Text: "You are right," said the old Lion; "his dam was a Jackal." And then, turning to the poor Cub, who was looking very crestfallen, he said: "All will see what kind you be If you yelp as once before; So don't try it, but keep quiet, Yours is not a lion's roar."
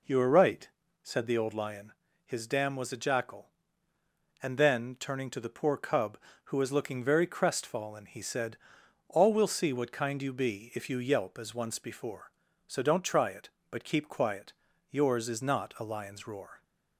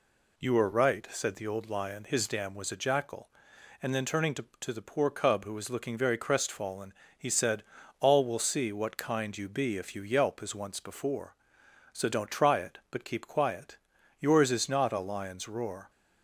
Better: first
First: none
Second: says "to" twice; at 4.5 s

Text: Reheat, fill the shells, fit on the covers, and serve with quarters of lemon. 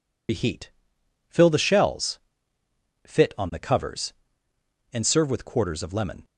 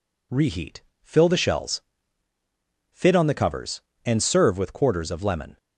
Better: second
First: loses the start of "Reheat"; at 0.2 s; 100 ms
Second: none

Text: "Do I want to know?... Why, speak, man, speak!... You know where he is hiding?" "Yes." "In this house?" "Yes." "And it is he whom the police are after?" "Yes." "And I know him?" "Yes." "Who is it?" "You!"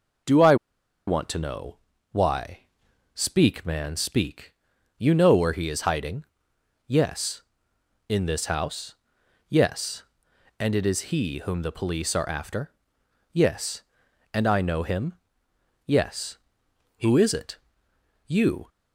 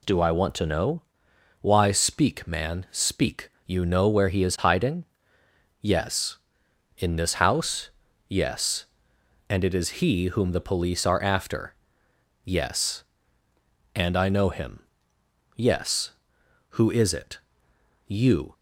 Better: second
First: pauses between "I" and "want"; noticeable; at 0.5 s; 0.52 s long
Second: none

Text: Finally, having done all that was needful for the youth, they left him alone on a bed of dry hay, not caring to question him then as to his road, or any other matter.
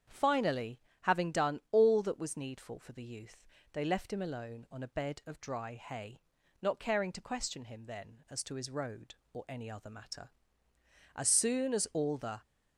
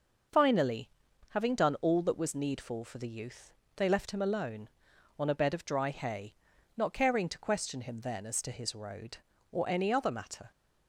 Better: second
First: starts louder than the rest; strong; until 1.3 s; 8 dB // goes on to say "As soon as all the"; noticeable; from 11.1 s on; 1.2 s long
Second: none

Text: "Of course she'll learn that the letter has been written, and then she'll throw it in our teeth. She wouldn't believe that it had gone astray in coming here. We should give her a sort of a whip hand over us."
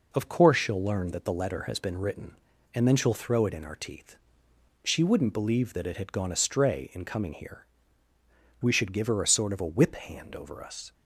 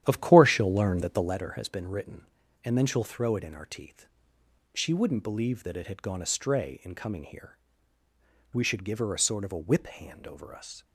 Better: first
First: none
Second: starts louder than the rest; strong; until 1.5 s; 11 dB

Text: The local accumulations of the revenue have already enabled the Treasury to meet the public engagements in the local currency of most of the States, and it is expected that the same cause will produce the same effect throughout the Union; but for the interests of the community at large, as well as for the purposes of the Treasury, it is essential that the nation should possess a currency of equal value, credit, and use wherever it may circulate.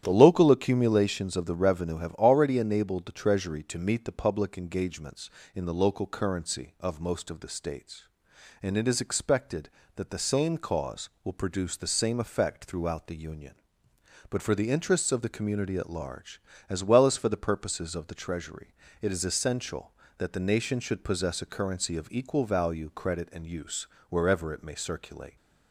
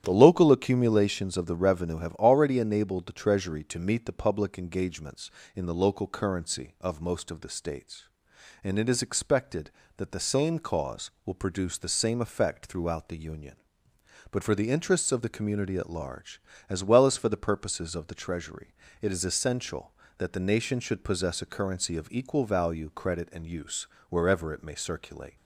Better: neither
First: starts louder than the rest; strong; until 1.0 s; 11 dB // pauses between "use" and "wherever"; slight; at 23.8 s; 0.22 s long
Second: starts louder than the rest; strong; until 1.0 s; 11 dB // pauses between "use" and "wherever"; slight; at 23.8 s; 0.22 s long

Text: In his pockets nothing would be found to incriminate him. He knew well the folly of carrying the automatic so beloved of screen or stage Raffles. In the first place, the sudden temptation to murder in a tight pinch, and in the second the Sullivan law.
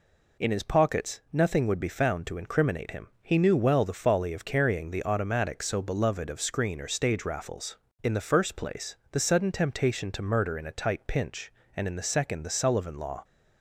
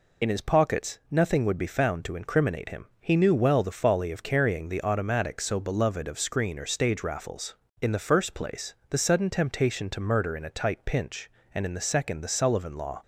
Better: first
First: none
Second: loses the start of "In"; at 0.2 s; 35 ms

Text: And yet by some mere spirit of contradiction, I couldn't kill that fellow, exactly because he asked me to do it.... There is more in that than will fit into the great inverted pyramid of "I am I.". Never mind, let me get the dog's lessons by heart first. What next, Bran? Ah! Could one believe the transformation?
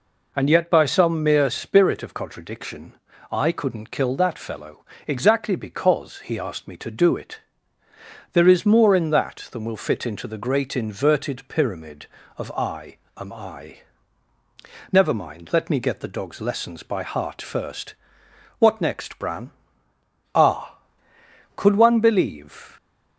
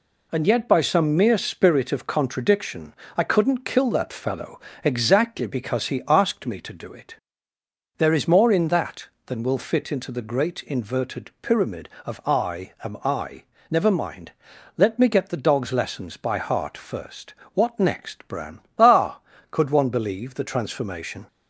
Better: second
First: pauses between "I" and "am"; slight; at 12.9 s; 0.18 s long // stops before "the transformation"; at 22.7 s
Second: none

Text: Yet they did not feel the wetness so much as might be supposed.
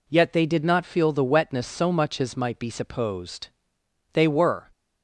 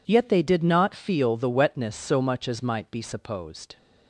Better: second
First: goes on to say "They were"; from 4.1 s on; 0.56 s long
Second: none

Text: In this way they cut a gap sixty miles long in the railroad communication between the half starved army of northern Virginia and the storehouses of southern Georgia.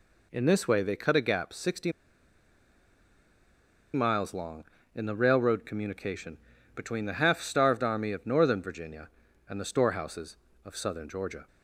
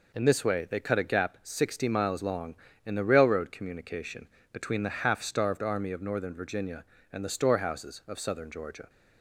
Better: second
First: pauses between "sixty" and "miles"; strong; at 1.9 s; 2.0 s long // pauses between "communication" and "between"; at 6.3 s; 0.38 s long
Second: pauses between "communication" and "between"; slight; at 4.2 s; 0.24 s long

